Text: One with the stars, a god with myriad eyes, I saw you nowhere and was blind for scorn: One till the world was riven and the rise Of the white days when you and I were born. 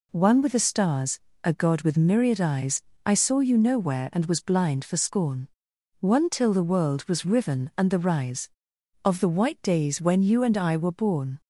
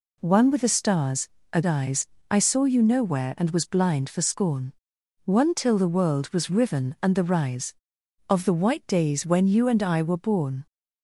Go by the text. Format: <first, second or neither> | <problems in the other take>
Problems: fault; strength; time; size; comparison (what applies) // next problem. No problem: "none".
first | skips "god with myriad"; at 1.6 s